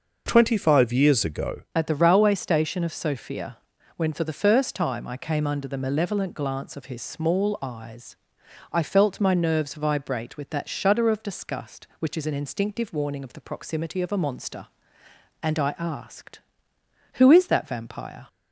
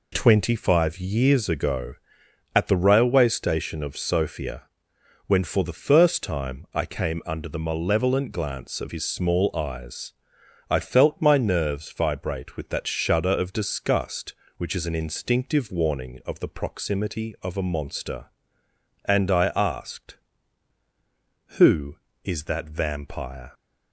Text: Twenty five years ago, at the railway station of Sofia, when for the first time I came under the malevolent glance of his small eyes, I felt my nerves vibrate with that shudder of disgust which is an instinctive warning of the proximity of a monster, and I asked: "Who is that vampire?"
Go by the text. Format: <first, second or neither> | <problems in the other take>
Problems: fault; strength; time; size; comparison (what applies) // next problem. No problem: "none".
second | changes voice at "at"; from 1.7 s on; 16.5 s long